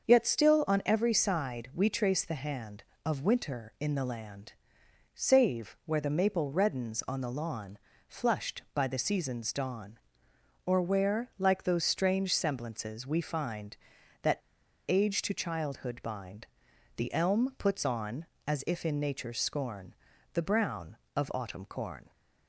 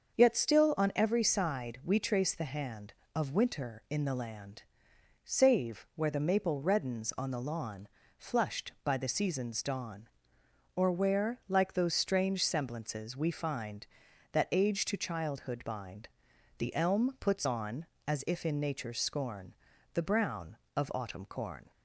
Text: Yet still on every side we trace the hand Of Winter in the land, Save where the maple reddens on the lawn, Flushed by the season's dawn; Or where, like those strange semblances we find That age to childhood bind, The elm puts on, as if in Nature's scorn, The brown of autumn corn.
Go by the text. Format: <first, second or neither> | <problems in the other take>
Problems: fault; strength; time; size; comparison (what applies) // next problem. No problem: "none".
second | starts louder than the rest; until 1.1 s; 6.5 dB; also in the second // pauses between "That" and "age"; noticeable; at 14.3 s; 0.50 s long